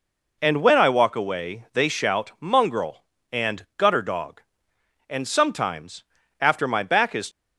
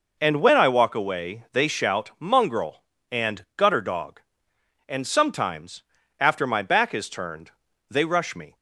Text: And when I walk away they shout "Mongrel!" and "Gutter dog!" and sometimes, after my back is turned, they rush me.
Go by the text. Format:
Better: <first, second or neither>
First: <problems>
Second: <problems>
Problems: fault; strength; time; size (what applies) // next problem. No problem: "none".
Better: second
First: stops before "turned they rush me"; at 7.3 s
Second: none